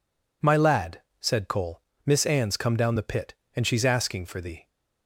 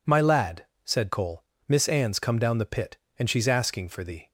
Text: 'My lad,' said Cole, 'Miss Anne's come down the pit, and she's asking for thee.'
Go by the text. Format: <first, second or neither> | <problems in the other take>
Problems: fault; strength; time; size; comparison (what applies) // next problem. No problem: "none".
neither | none